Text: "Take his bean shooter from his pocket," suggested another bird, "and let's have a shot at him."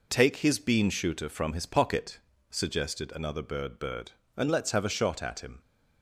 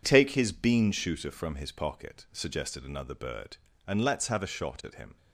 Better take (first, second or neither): second